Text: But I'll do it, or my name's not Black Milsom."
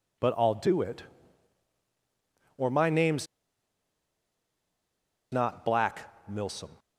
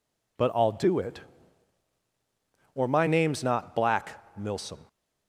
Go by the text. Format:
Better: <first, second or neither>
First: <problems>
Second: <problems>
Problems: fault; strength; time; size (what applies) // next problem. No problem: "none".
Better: second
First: pauses between "name's" and "not"; strong; at 3.2 s; 2.0 s long // pauses between "Black" and "Milsom"; slight; at 5.9 s; 0.28 s long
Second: pauses between "Black" and "Milsom"; slight; at 4.0 s; 0.26 s long